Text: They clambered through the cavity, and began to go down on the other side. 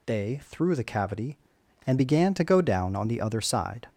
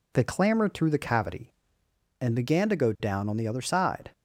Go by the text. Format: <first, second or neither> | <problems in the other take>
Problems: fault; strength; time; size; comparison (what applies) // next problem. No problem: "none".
second | skips "clambered"; at 0.4 s